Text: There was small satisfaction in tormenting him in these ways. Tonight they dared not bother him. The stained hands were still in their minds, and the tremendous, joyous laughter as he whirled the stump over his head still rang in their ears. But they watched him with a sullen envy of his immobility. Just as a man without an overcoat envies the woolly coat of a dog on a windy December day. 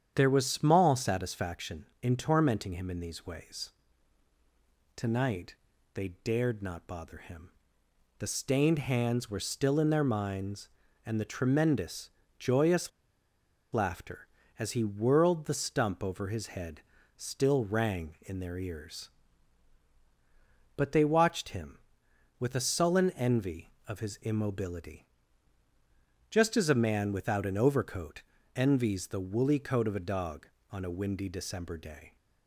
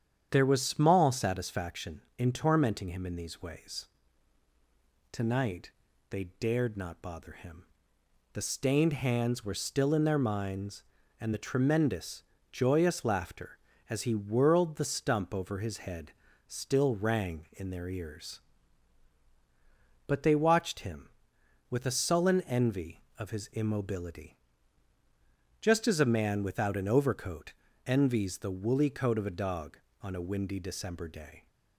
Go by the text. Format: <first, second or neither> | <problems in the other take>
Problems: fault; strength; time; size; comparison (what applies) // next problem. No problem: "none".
second | starts louder than the rest; strong; until 1.1 s; 8.5 dB; strong in the second // pauses between "Tonight" and "they"; at 5.5 s; 0.40 s long; also in the second // pauses between "joyous" and "laughter"; noticeable; at 12.9 s; 0.83 s long // pauses between "head" and "still"; at 16.7 s; 0.38 s long; also in the second // pauses between "overcoat" and "envies"; slight; at 28.2 s; 0.34 s long; slight in the second